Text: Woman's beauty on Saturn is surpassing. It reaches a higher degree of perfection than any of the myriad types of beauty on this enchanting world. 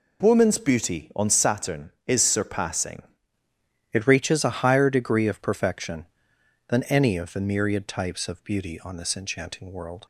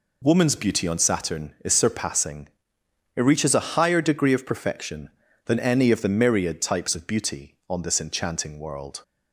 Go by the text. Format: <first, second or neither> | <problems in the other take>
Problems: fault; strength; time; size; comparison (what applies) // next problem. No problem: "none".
second | changes voice at "It"; from 3.9 s on; 6.1 s long